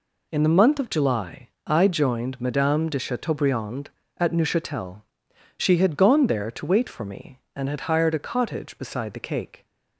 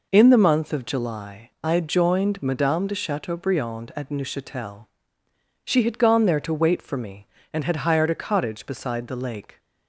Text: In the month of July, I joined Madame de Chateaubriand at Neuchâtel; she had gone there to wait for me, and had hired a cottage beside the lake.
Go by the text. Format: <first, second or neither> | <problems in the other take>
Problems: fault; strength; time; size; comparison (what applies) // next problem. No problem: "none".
second | says "cake" for "lake"; at 9.2 s